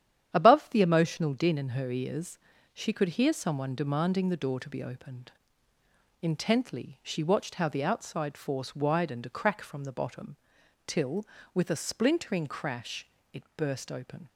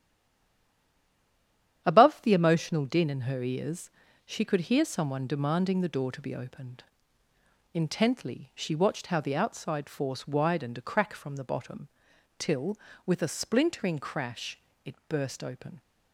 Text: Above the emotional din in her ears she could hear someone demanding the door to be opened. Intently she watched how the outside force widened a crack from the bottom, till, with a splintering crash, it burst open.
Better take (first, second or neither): first